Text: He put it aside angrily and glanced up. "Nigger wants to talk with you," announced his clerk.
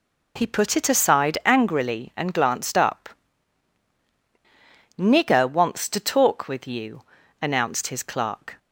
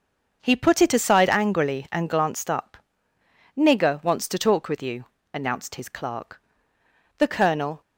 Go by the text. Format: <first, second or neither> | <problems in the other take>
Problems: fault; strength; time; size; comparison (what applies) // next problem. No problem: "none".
first | starts louder than the rest; until 1.4 s; 6.5 dB // goes on to say "The Colonel"; noticeable; from 7.1 s on; 0.64 s long